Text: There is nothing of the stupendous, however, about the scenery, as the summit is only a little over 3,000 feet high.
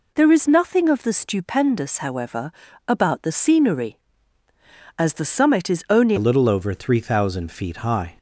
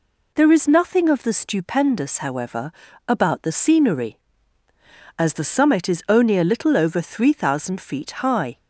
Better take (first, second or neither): second